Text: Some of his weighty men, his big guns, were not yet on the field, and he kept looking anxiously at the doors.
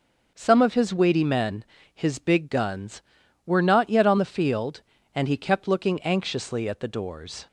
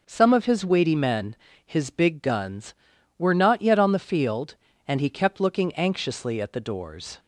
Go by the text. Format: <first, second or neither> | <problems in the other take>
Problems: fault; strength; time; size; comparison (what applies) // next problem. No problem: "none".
neither | none